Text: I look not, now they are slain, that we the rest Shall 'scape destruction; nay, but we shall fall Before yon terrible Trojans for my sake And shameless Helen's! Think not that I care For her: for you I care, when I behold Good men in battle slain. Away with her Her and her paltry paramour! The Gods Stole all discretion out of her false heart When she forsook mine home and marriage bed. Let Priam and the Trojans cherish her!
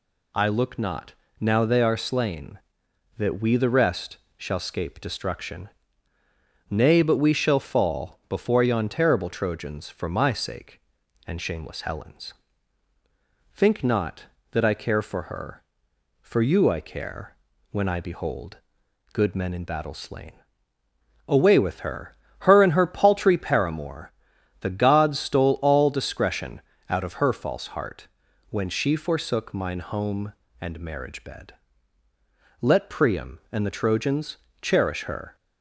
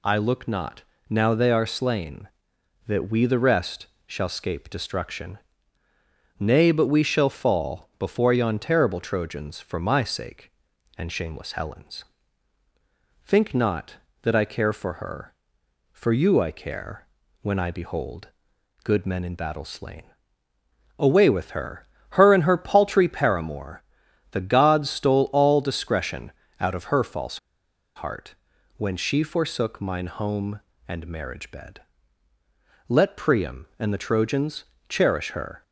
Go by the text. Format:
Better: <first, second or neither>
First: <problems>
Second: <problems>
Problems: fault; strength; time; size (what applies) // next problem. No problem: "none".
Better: first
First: pauses between "rest" and "Shall"; slight; at 4.1 s; 0.22 s long // pauses between "behold" and "Good"; noticeable; at 18.5 s; 0.56 s long // pauses between "her" and "Her"; slight; at 22.1 s; 0.24 s long // pauses between "discretion" and "out"; slight; at 26.6 s; 0.28 s long // pauses between "heart" and "When"; at 28.0 s; 0.42 s long // pauses between "Trojans" and "cherish"; slight; at 34.3 s; 0.24 s long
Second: pauses between "rest" and "Shall"; slight; at 3.8 s; 0.22 s long // pauses between "behold" and "Good"; noticeable; at 18.2 s; 0.56 s long // pauses between "her" and "Her"; slight; at 21.8 s; 0.24 s long // pauses between "discretion" and "out"; slight; at 26.3 s; 0.28 s long // pauses between "false" and "heart"; noticeable; at 27.3 s; 0.57 s long // pauses between "heart" and "When"; at 28.3 s; 0.42 s long // pauses between "Trojans" and "cherish"; slight; at 34.6 s; 0.24 s long